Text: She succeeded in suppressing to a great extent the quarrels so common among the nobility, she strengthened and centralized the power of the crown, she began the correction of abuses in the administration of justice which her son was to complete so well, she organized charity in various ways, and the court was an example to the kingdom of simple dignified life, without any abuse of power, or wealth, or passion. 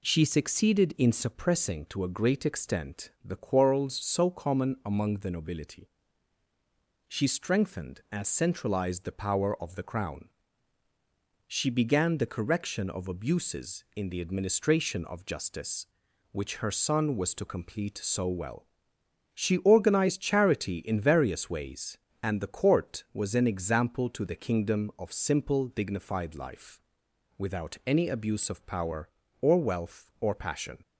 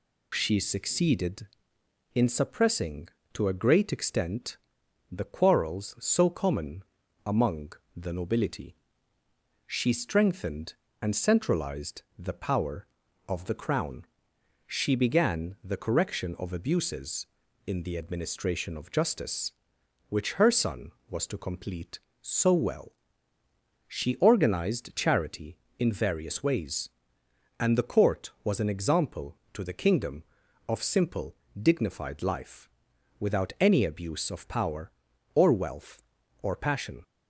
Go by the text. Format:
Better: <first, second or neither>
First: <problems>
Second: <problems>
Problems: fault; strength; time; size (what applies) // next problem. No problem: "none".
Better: first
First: none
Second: loses the start of "She"; at 0.3 s; 25 ms // pauses between "extent" and "the"; noticeable; at 4.5 s; 0.54 s long // pauses between "common" and "among"; at 6.8 s; 0.42 s long // pauses between "among" and "the"; slight; at 7.7 s; 0.24 s long // pauses between "simple" and "dignified"; slight; at 31.3 s; 0.26 s long